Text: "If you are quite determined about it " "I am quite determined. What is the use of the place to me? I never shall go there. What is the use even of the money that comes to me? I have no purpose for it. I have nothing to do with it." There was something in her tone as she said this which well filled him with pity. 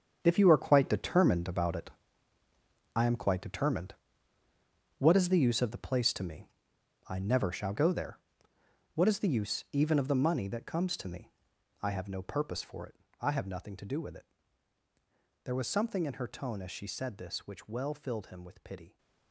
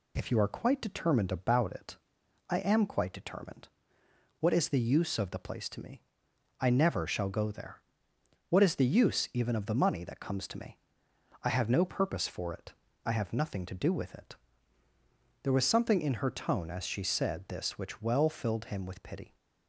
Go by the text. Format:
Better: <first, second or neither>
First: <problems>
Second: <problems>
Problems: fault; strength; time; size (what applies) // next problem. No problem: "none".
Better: second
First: gets quieter; noticeable; throughout; 6 dB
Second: none